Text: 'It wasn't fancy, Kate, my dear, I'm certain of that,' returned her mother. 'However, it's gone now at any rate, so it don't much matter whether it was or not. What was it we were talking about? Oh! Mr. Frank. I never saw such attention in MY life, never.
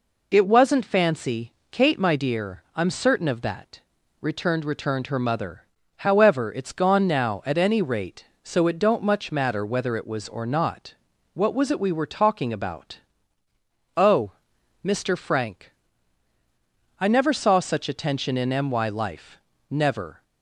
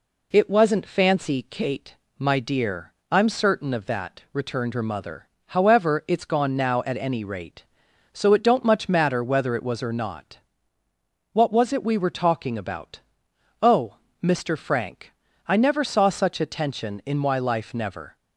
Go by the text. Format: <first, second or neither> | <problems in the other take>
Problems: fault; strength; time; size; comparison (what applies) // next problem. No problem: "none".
second | says "returned" twice; at 4.6 s